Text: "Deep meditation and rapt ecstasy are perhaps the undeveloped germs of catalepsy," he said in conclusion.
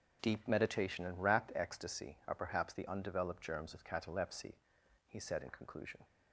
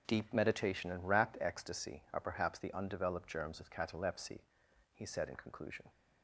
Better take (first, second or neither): neither